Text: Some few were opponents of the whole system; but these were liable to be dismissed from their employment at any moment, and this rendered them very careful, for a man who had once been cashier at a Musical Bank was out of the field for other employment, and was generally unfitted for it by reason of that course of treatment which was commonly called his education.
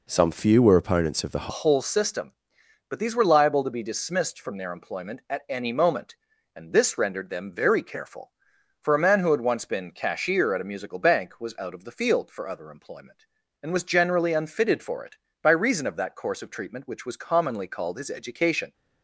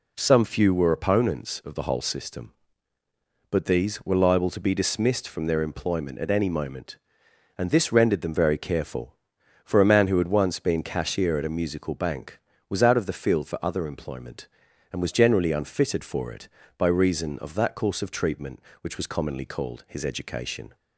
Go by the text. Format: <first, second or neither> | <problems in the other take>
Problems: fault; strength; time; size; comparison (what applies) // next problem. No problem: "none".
second | changes voice at "whole"; from 1.4 s on; 17.3 s long